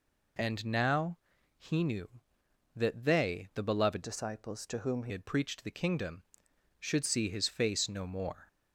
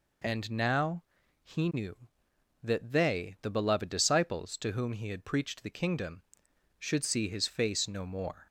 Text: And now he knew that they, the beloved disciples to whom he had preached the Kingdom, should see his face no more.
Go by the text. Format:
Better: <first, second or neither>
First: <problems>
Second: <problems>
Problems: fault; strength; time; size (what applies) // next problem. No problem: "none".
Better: second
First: pauses between "now" and "he"; at 1.1 s; 0.40 s long // changes voice from "disciples" to "he"; from 4.0 to 5.1 s; 1.1 s long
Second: pauses between "now" and "he"; at 1.0 s; 0.40 s long